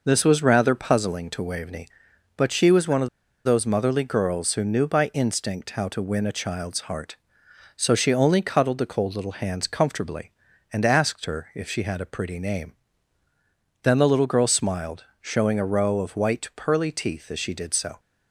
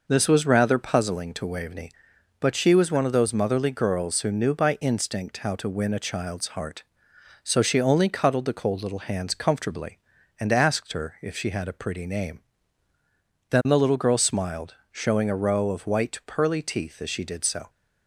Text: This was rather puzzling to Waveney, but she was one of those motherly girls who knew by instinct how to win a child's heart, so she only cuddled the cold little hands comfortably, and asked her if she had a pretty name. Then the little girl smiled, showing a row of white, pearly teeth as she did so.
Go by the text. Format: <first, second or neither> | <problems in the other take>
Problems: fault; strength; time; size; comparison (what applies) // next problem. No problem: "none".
second | pauses between "of" and "those"; at 3.0 s; 0.36 s long